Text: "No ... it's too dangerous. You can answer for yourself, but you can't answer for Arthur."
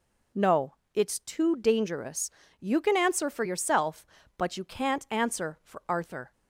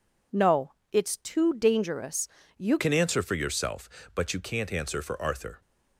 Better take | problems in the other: first | changes voice at "can"; from 2.7 s on; 2.9 s long

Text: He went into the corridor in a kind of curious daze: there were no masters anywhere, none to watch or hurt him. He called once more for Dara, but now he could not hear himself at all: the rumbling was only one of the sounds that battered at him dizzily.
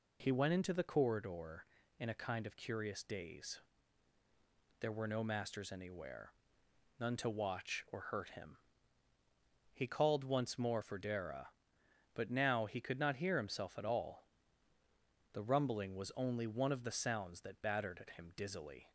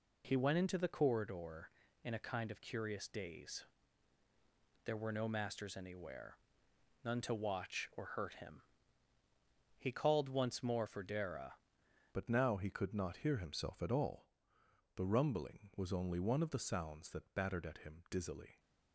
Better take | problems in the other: first | changes voice at "but"; from 12.1 s on; 6.4 s long

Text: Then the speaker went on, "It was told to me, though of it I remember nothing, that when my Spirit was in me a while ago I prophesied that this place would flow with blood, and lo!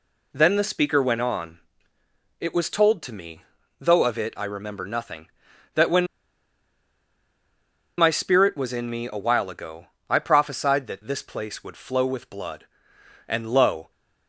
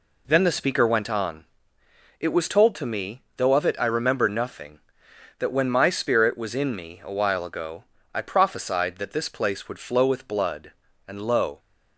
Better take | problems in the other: second | pauses between "when" and "my"; strong; at 6.0 s; 1.9 s long // pauses between "ago" and "I"; slight; at 9.8 s; 0.24 s long; slight in the second

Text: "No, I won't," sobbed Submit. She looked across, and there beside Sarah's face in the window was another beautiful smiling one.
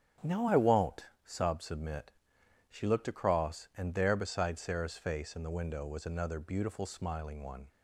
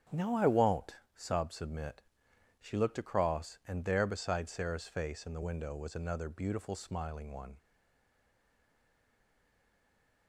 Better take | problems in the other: first | starts louder than the rest; strong; until 1.2 s; 8 dB; strong in the first // stays silent after the last word; strong; from 7.5 s on; 2.7 s long

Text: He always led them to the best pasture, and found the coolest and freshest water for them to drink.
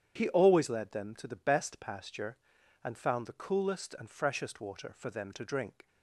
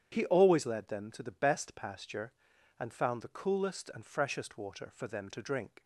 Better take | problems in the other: neither | starts louder than the rest; strong; the same in both

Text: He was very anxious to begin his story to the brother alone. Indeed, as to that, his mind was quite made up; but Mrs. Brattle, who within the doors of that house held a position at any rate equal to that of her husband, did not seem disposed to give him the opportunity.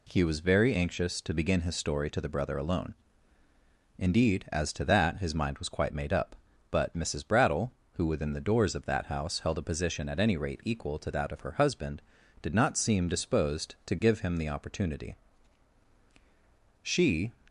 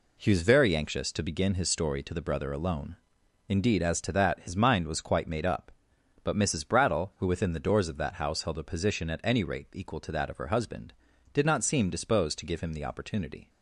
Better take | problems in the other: second | goes on to say "She"; from 16.8 s on; 0.50 s long

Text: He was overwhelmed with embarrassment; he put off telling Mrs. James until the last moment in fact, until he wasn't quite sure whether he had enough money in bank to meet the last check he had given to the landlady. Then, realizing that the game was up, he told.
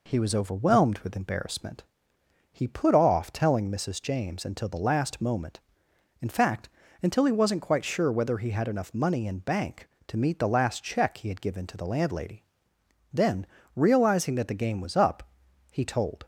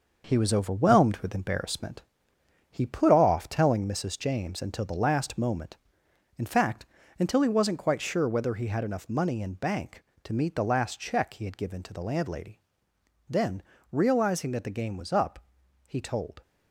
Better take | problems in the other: first | gets quieter; throughout; 7 dB

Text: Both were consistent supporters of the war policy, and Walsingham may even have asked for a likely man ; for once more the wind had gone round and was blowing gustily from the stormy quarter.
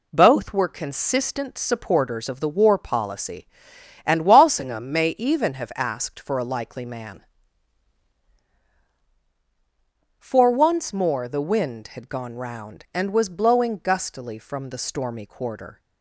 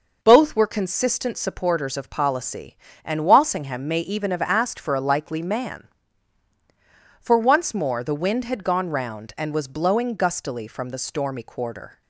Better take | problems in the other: first | skips "the war"; at 2.1 s

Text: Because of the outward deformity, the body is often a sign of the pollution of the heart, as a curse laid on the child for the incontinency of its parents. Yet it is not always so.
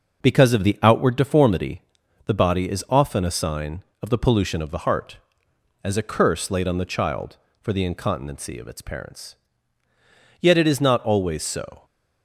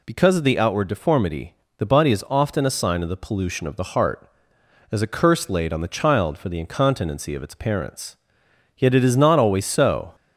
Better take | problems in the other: neither | none

